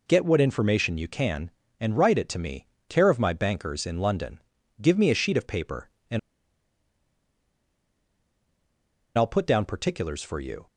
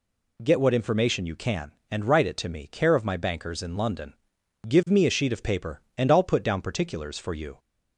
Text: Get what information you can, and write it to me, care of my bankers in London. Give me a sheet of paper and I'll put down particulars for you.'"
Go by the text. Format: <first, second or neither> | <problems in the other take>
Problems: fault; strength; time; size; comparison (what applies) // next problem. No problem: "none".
second | pauses between "and" and "I'll"; strong; at 6.1 s; 2.9 s long